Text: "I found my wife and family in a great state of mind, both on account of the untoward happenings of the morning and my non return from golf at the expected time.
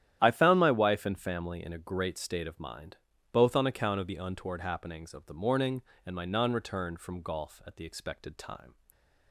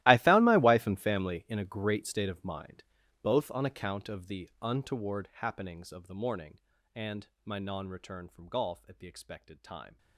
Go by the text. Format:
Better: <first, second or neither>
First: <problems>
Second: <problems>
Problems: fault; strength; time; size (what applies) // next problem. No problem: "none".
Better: first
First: starts louder than the rest; strong; until 1.2 s; 11 dB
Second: gets quieter; strong; throughout; 20 dB // starts louder than the rest; strong; until 1.0 s; 16 dB // pauses between "and" and "my"; slight; at 7.2 s; 0.18 s long